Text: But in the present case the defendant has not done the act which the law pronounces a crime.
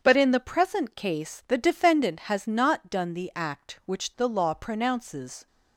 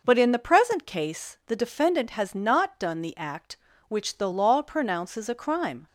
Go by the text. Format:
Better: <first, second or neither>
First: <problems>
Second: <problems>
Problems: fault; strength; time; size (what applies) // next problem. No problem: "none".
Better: second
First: starts louder than the rest; strong; until 1.0 s; 7 dB // stops before "a crime"; at 5.4 s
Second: none